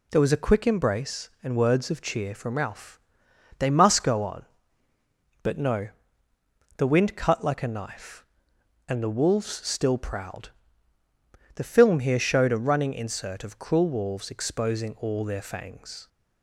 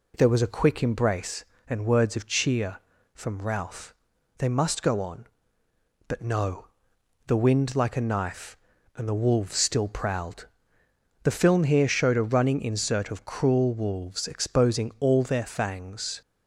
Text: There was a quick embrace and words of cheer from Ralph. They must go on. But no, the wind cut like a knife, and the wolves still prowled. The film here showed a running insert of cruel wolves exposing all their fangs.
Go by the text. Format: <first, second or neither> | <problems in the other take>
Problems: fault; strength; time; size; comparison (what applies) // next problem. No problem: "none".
first | skips "cut"; at 7.7 s